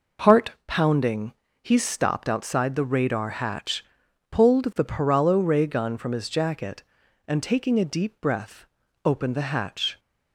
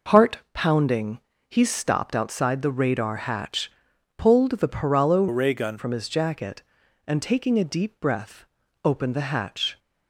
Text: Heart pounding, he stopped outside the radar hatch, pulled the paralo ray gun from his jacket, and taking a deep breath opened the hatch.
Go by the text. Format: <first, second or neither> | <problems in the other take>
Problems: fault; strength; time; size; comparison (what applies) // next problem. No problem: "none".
first | pauses between "Heart" and "pounding"; slight; at 0.3 s; 0.16 s long; slight in the first // changes voice from "ray" to "gun"; from 5.2 to 5.7 s; 0.5 s long // pauses between "breath" and "opened"; at 8.4 s; 0.38 s long; also in the first